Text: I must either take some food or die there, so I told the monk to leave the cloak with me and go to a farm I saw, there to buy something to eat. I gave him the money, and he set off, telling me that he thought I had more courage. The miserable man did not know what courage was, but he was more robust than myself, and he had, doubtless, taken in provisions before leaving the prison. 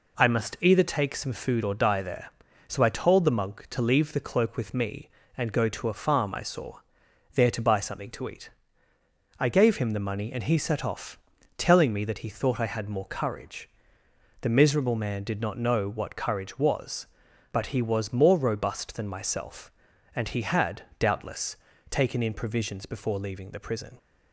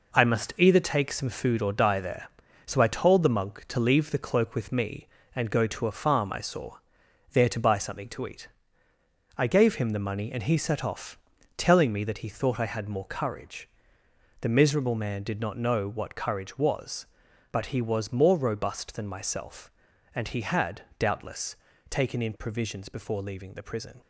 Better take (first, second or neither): first